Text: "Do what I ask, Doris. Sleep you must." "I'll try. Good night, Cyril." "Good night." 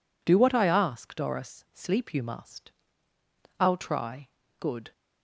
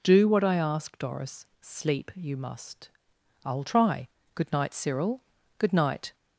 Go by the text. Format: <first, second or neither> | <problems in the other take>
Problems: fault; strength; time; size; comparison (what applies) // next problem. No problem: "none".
second | stops before "night Cyril Good night"; at 4.9 s